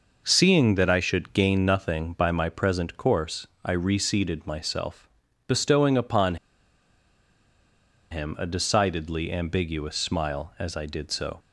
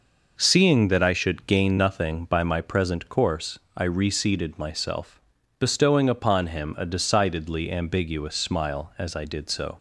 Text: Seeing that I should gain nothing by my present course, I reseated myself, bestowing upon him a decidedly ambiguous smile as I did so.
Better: second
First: pauses between "upon" and "him"; strong; at 6.3 s; 1.7 s long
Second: none

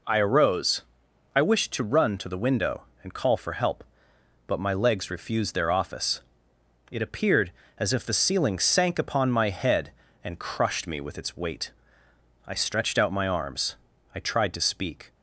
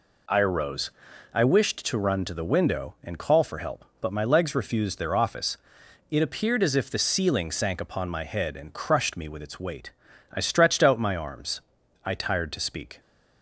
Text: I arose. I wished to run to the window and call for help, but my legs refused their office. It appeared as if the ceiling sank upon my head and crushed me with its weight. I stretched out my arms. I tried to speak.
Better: first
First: none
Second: says "tired" for "tried"; at 12.1 s

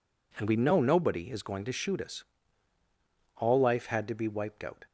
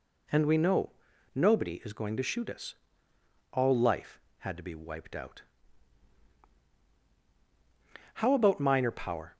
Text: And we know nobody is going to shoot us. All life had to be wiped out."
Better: first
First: none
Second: pauses between "know" and "nobody"; at 0.8 s; 0.44 s long // goes on to say "How about minor power"; noticeable; from 8.1 s on; 1.2 s long

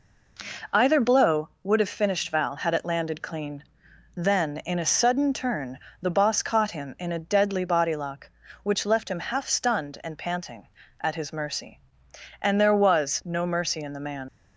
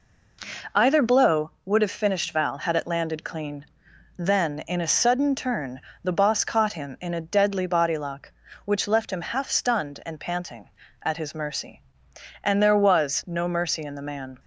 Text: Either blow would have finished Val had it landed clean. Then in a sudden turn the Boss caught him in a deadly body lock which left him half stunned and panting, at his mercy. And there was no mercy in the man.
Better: second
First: pauses between "turn" and "the"; slight; at 5.7 s; 0.20 s long // leaves "man" unfinished; at 14.2 s; 90 ms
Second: pauses between "turn" and "the"; slight; at 5.8 s; 0.20 s long

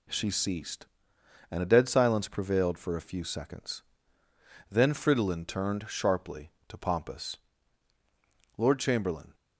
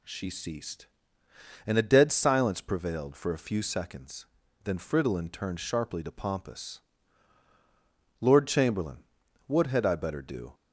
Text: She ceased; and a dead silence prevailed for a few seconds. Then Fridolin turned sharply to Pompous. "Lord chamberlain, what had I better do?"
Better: second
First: stops before "what had I better do"; at 9.3 s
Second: none

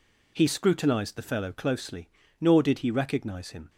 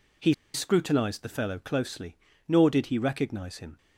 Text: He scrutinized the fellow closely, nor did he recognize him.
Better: first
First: none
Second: pauses between "He" and "scrutinized"; slight; at 0.3 s; 0.20 s long

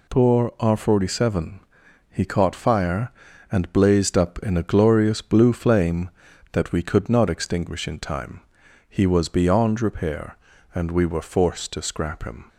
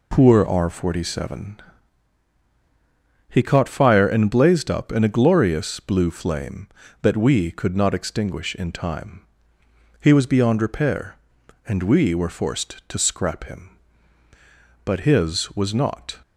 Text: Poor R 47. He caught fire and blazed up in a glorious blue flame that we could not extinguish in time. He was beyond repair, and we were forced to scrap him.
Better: first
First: none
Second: goes on to say "But his was not"; from 14.8 s on; 1.3 s long

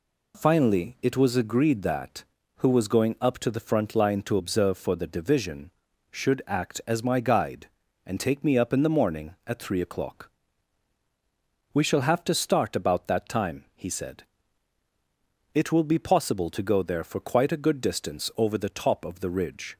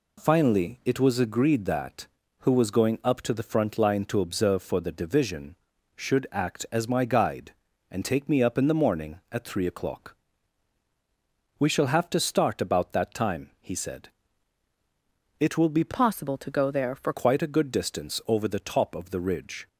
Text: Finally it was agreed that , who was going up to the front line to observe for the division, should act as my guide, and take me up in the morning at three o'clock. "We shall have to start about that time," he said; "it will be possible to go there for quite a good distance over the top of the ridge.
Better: first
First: none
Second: changes voice from "possible" to "for"; from 15.9 to 17.1 s; 1.2 s long

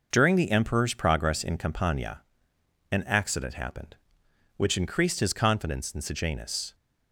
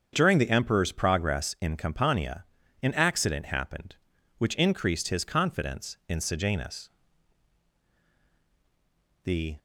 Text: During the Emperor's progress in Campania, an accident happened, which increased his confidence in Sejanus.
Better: first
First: none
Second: starts louder than the rest; strong; until 1.1 s; 7 dB // goes on to say "The"; slight; from 9.2 s on; 0.32 s long

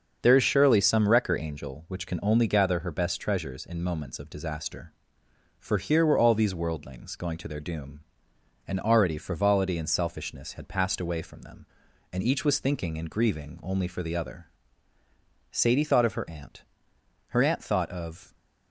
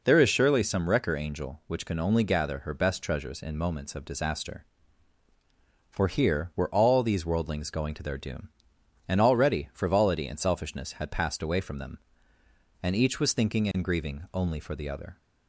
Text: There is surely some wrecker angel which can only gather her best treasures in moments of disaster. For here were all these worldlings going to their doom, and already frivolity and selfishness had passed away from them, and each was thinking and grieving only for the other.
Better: second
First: starts louder than the rest; until 1.2 s; 6.5 dB // goes on to say "Sadie thought of her aunt her aunt thought of"; strong; from 15.5 s on; 2.8 s long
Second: none

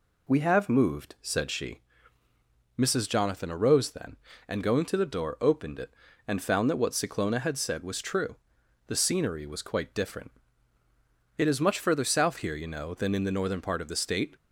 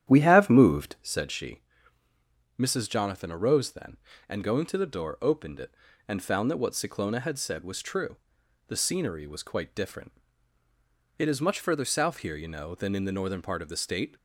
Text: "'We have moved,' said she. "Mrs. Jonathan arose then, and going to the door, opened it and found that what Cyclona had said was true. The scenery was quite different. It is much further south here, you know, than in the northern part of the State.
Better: first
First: none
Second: starts louder than the rest; strong; until 1.1 s; 10.5 dB

